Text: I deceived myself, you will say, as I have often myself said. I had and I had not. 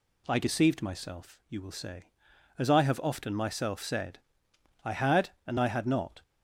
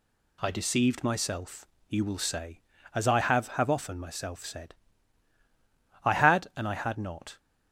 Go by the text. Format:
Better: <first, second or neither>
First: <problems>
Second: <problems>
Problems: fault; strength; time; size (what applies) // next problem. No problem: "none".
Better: first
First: none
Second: says "have" twice; at 3.4 s